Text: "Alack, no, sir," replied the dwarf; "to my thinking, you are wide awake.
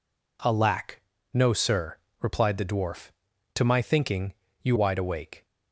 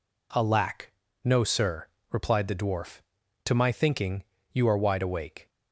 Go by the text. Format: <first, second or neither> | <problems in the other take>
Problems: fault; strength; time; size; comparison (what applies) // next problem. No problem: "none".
second | skips "are"; at 4.7 s